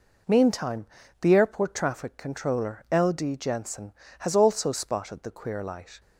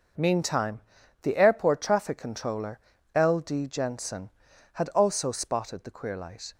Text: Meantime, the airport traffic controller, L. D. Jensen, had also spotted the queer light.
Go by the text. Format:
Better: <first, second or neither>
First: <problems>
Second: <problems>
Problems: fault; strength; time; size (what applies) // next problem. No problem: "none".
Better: second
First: says "has" for "had"; at 4.1 s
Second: none